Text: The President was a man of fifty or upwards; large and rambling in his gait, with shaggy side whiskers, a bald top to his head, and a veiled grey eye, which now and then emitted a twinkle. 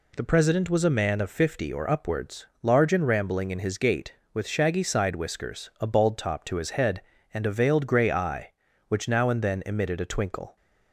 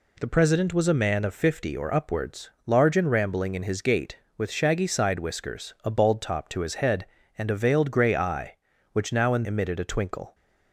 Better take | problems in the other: first | skips "then"; at 9.4 s

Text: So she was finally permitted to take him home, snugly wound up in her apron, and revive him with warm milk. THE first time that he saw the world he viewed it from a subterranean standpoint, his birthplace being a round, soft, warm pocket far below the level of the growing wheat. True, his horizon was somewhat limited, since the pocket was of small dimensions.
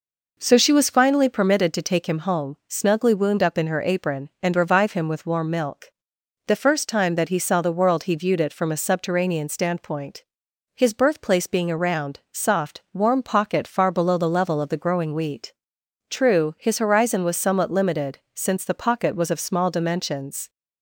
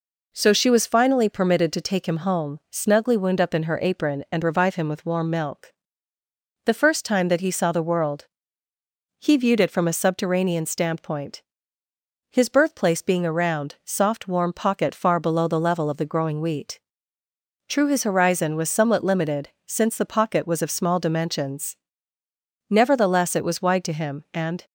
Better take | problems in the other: first | pauses between "world" and "he"; noticeable; at 8.2 s; 0.96 s long // goes on to say "Nevertheless it was wide to him and"; strong; from 22.6 s on; 1.9 s long

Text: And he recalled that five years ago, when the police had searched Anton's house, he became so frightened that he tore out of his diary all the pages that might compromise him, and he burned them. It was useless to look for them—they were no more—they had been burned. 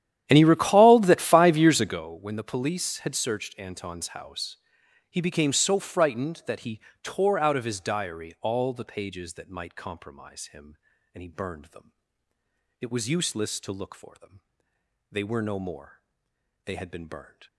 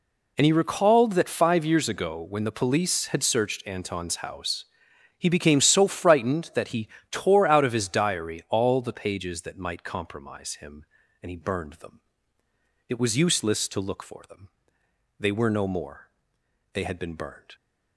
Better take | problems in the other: second | starts louder than the rest; strong; until 2.0 s; 11 dB // pauses between "he" and "tore"; slight; at 6.8 s; 0.22 s long; slight in the second

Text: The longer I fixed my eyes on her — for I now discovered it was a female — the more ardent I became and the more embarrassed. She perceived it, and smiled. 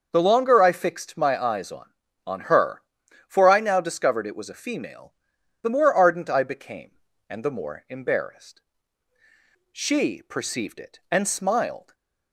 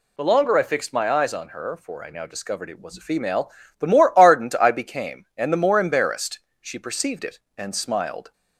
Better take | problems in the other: second | starts louder than the rest; until 1.1 s; 6.5 dB // says "on" twice; at 2.2 s // stays silent after the last word; slight; from 11.8 s on; 0.5 s long

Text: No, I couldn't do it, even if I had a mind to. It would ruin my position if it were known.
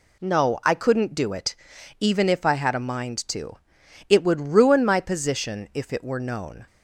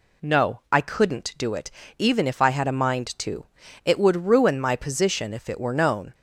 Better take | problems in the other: neither | none

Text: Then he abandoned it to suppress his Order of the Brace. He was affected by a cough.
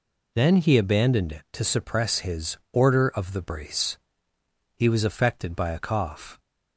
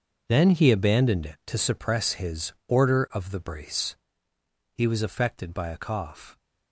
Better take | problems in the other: first | gets quieter; strong; throughout; 14 dB

